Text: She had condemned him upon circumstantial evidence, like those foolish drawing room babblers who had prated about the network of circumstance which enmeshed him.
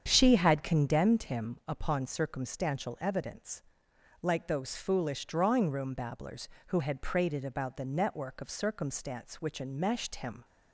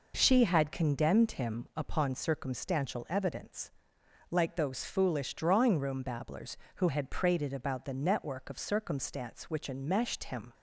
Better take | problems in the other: second | starts louder than the rest; strong; until 1.2 s; 8 dB

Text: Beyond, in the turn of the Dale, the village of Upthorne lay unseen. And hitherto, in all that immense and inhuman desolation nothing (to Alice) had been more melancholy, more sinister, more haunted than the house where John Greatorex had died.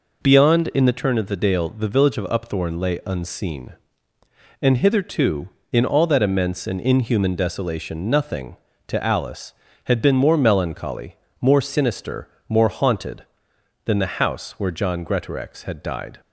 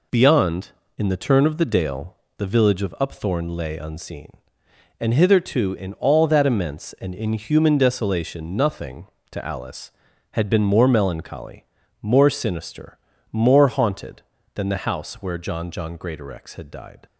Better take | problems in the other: first | says "John" twice; at 15.6 s

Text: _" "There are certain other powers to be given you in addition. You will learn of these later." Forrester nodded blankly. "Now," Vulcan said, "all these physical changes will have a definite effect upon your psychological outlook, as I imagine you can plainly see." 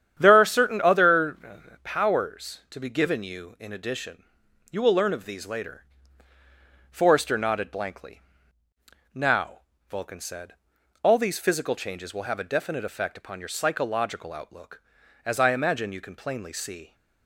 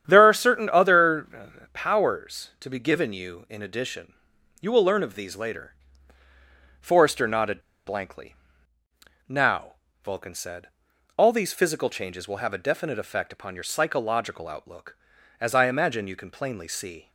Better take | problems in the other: first | starts louder than the rest; strong; until 1.0 s; 9.5 dB; strong in the first // pauses between "other" and "powers"; slight; at 1.4 s; 0.24 s long; slight in the first // pauses between "nodded" and "blankly"; slight; at 7.5 s; 0.26 s long

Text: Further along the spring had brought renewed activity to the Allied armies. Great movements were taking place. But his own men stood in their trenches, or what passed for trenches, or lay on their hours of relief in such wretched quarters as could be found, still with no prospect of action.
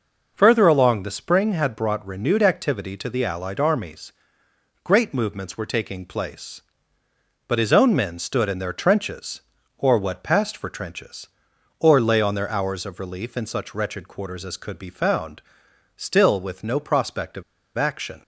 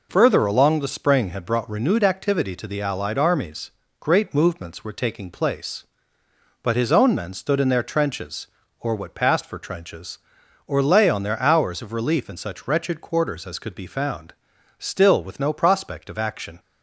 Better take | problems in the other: second | pauses between "of" and "action"; slight; at 17.4 s; 0.34 s long

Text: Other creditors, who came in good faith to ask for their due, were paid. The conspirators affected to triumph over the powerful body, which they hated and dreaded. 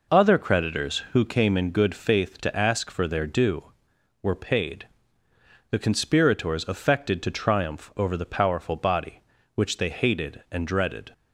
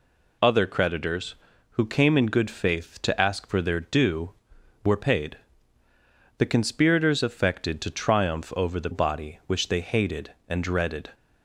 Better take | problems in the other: first | skips "powerful"; at 8.9 s

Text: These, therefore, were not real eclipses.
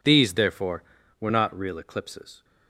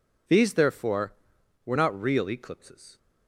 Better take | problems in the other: neither | none

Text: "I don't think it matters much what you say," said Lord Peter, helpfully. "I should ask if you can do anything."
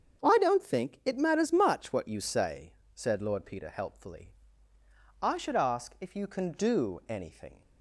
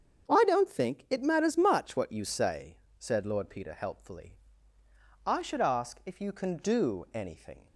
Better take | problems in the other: neither | starts louder than the rest; strong; the same in both

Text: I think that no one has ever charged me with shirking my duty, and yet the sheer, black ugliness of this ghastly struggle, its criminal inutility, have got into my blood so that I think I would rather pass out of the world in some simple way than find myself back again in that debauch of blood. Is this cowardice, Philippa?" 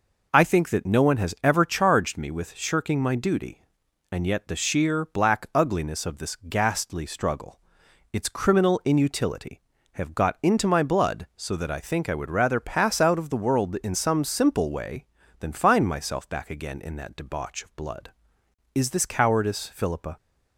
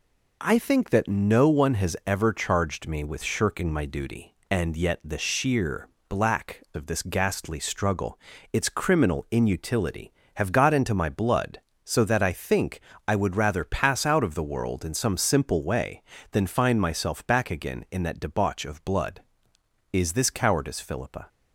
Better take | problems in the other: first | skips "ugliness"; at 6.6 s // pauses between "think" and "I"; slight; at 12.7 s; 0.28 s long

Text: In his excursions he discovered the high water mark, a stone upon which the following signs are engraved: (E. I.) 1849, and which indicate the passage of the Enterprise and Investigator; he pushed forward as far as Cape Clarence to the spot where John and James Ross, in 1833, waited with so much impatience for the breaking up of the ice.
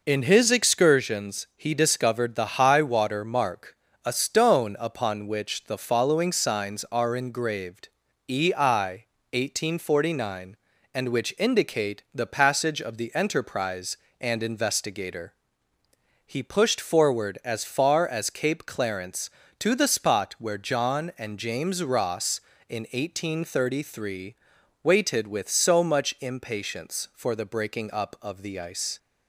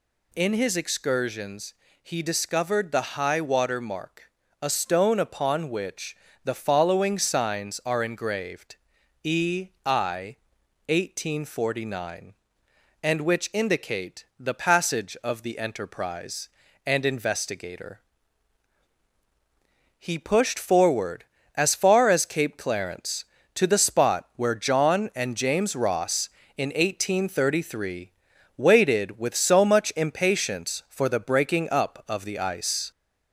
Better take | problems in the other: first | gets louder; slight; throughout; 2.5 dB // pauses between "excursions" and "he"; slight; at 1.7 s; 0.28 s long // pauses between "which" and "the"; slight; at 6.1 s; 0.28 s long

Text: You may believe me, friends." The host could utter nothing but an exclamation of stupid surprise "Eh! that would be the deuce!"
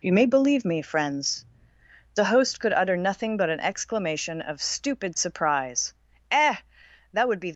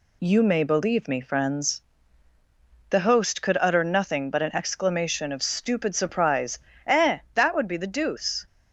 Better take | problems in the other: second | pauses between "surprise" and "Eh"; slight; at 5.9 s; 0.36 s long; slight in the second // stops before "the deuce"; at 7.5 s

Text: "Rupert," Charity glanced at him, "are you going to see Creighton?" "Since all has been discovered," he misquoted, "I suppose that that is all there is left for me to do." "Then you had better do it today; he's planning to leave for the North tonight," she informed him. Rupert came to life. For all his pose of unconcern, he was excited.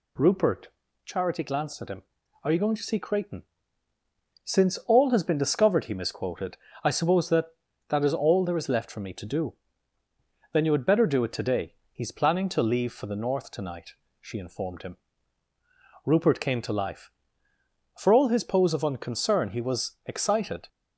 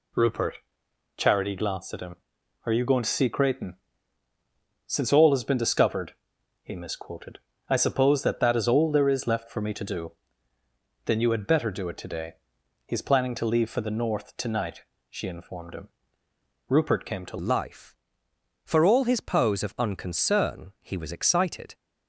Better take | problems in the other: first | changes voice at "life"; from 17.3 s on; 4.4 s long

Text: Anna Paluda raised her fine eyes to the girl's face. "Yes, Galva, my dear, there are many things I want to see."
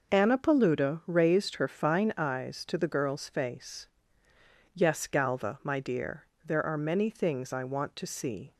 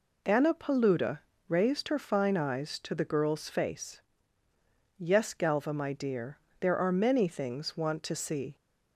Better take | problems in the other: first | pauses between "Paluda" and "raised"; slight; at 1.1 s; 0.30 s long // skips "I"; at 7.7 s

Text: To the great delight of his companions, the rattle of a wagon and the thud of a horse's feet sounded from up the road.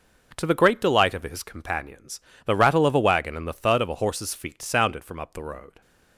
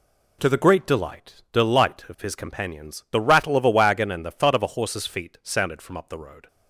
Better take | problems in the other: first | says "delight" twice; at 1.5 s

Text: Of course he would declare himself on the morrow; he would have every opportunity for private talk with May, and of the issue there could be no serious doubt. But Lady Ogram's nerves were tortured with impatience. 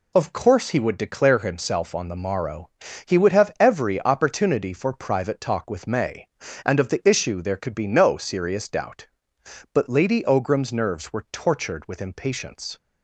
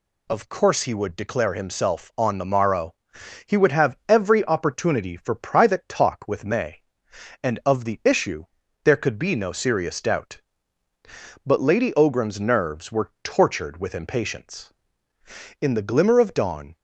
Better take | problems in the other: first | pauses between "issue" and "there"; at 8.4 s; 0.38 s long // goes on to say "In the glimmer of dawn"; noticeable; from 15.5 s on; 1.1 s long

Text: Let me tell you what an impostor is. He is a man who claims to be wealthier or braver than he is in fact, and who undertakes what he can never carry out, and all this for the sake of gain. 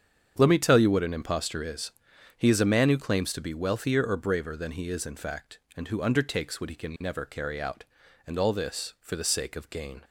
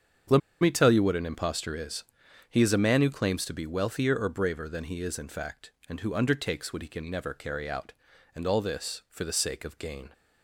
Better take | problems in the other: first | starts louder than the rest; strong; until 1.5 s; 7.5 dB; strong in the first // pauses between "Let" and "me"; slight; at 0.4 s; 0.21 s long

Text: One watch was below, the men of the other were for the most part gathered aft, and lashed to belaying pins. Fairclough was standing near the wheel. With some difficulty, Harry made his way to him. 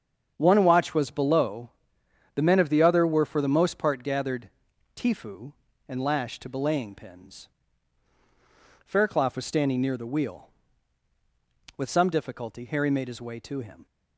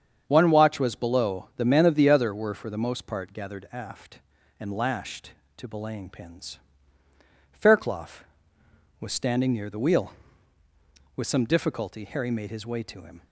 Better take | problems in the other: second | starts louder than the rest; strong; until 1.3 s; 7.5 dB; strong in the second // says "tifu" for "aft"; at 4.9 s

